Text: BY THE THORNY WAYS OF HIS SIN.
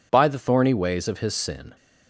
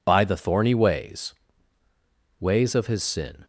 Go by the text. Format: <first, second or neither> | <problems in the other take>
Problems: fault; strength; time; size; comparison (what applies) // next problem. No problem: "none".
first | says "WAYS" twice; at 2.3 s